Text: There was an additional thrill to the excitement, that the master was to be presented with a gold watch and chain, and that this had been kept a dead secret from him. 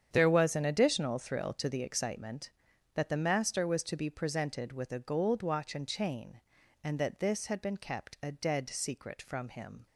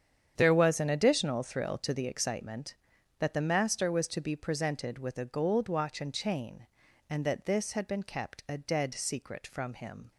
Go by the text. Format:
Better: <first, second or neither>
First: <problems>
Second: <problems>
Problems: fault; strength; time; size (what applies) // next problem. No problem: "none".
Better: neither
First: starts louder than the rest; strong; until 1.1 s; 8.5 dB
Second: starts louder than the rest; strong; until 1.3 s; 8.5 dB